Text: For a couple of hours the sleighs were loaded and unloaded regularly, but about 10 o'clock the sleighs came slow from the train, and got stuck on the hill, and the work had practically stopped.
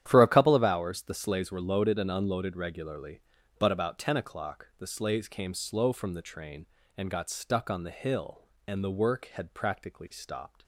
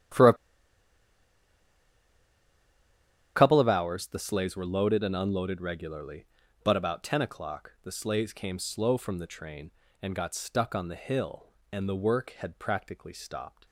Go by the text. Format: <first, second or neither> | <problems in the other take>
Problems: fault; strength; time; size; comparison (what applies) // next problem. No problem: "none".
first | starts louder than the rest; strong; until 4.1 s; 10.5 dB; strong in the first // pauses between "a" and "couple"; strong; at 0.3 s; 3.0 s long